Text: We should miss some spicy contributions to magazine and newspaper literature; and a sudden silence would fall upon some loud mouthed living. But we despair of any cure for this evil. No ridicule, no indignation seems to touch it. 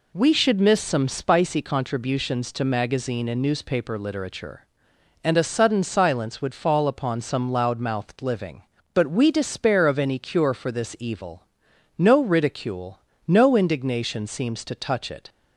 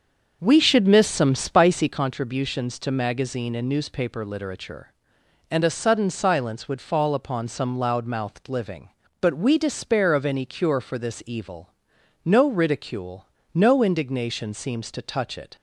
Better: first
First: none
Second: starts louder than the rest; until 2.0 s; 6.5 dB

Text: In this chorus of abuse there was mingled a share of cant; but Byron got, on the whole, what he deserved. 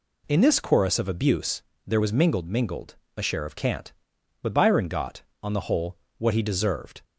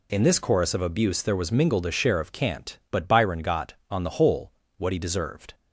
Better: second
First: pauses between "abuse" and "there"; slight; at 1.6 s; 0.24 s long // says "mingled" twice; at 2.4 s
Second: none

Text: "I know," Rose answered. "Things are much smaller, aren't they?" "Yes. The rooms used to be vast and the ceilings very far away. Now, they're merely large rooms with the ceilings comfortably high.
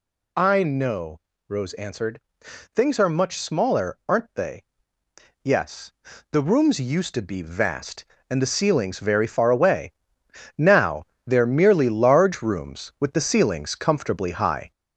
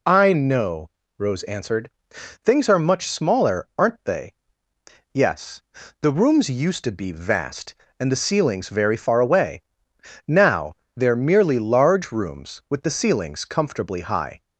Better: second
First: gets louder; noticeable; throughout; 5.5 dB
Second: none

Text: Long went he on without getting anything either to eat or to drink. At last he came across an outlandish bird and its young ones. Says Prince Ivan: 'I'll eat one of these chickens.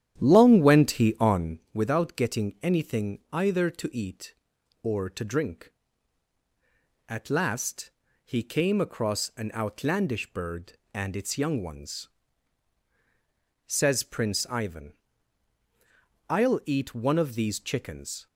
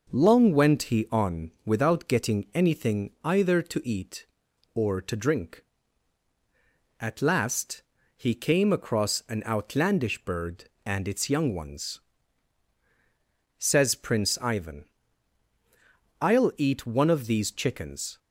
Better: second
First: starts louder than the rest; strong; until 1.6 s; 11 dB // pauses between "on" and "without"; slight; at 1.5 s; 0.16 s long // pauses between "last" and "he"; slight; at 7.9 s; 0.34 s long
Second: pauses between "on" and "without"; slight; at 1.5 s; 0.16 s long // pauses between "last" and "he"; slight; at 7.8 s; 0.34 s long

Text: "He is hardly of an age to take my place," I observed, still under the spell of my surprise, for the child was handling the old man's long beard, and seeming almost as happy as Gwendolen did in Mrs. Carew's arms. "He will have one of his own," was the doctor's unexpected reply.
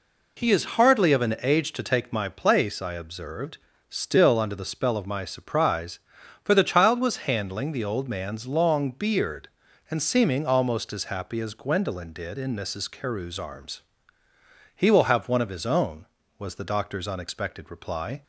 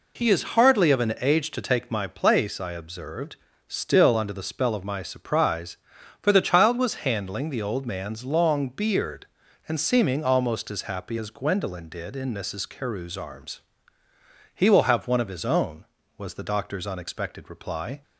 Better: neither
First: none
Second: none

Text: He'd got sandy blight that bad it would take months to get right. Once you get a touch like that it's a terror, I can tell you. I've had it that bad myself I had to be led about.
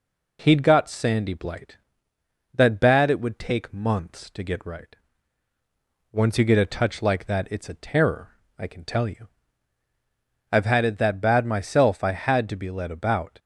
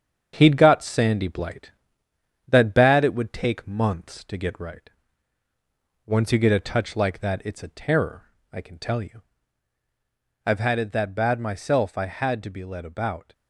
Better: first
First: none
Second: gets quieter; noticeable; throughout; 4.5 dB

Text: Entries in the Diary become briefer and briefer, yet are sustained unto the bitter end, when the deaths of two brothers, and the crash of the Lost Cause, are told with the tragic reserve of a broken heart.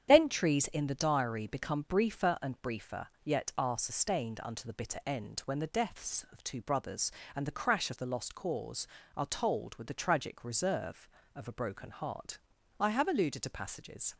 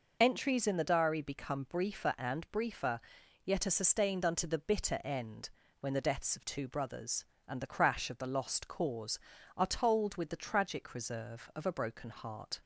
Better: second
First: starts louder than the rest; strong; until 1.1 s; 9 dB // goes on to say "I have alluded to passages"; from 12.7 s on; 1.3 s long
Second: none

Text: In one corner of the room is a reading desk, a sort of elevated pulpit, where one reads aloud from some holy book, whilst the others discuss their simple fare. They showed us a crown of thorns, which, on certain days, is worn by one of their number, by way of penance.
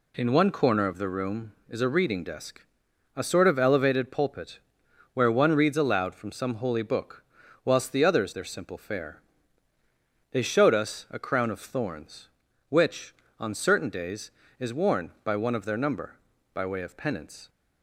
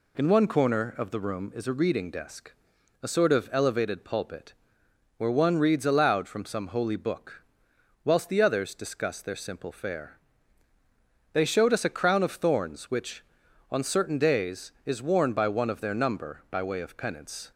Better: second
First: skips "discuss"; at 8.3 s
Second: none

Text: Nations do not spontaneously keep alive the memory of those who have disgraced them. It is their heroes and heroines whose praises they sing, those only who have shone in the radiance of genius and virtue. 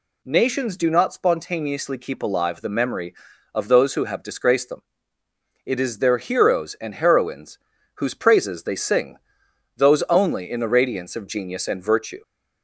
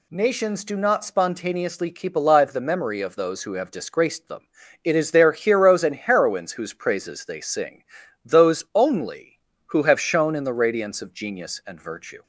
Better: second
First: pauses between "heroines" and "whose"; at 7.5 s; 0.38 s long // skips "who have shone"; at 10.4 s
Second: none

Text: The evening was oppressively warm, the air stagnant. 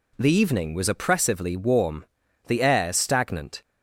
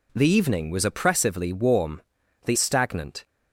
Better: first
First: none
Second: skips "air"; at 2.5 s

